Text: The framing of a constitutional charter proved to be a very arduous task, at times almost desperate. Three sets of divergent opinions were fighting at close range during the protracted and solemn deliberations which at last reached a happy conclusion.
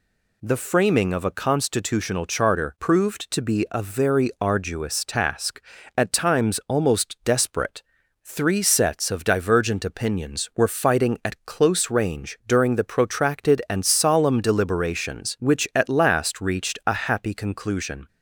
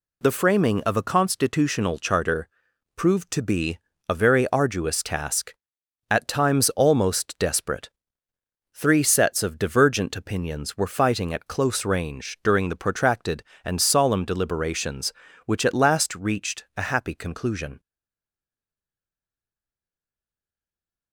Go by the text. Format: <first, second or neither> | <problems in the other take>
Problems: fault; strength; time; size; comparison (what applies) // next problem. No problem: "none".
first | pauses between "charter" and "proved"; noticeable; at 2.4 s; 0.46 s long // pauses between "be" and "a"; slight; at 3.7 s; 0.30 s long // stays silent after the last word; strong; from 17.7 s on; 3.4 s long